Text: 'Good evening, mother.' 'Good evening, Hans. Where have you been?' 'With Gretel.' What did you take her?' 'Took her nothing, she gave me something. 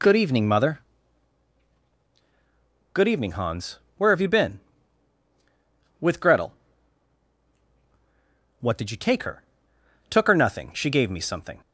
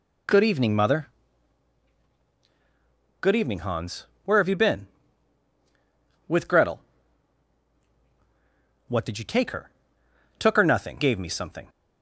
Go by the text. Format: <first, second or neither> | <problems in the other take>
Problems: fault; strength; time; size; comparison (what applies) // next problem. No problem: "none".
first | skips "she"; at 10.9 s